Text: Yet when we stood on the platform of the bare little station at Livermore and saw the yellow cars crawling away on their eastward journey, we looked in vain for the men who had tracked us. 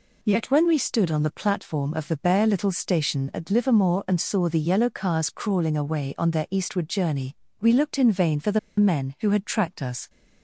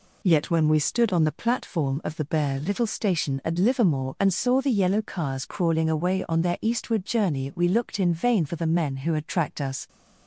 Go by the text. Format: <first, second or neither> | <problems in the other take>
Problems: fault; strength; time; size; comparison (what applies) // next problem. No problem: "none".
second | pauses between "the" and "men"; slight; at 8.5 s; 0.20 s long